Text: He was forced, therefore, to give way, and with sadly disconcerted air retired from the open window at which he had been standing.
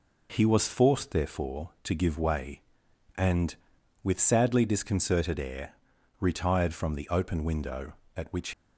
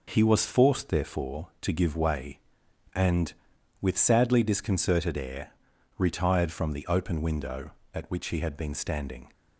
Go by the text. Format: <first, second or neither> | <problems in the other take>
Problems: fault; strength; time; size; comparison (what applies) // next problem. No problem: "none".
second | pauses between "air" and "retired"; noticeable; at 5.7 s; 0.48 s long; noticeable in the second // stops before "he had been standing"; at 8.5 s